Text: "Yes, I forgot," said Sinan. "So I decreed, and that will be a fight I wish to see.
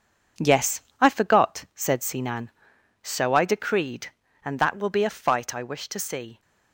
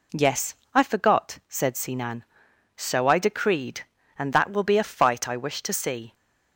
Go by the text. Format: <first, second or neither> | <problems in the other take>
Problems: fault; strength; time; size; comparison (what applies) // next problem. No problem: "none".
second | gets quieter; strong; throughout; 8 dB